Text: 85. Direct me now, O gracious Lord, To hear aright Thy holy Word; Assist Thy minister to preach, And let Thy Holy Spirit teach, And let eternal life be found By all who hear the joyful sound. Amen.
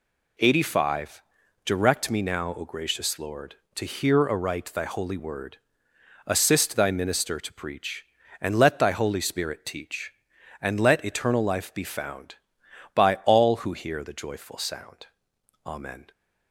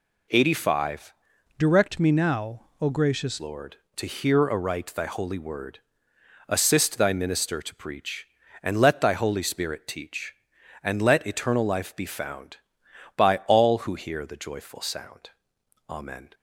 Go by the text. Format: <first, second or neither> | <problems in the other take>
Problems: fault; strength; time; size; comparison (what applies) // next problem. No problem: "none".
first | changes voice from "Direct" to "gracious"; from 1.5 to 3.3 s; 1.8 s long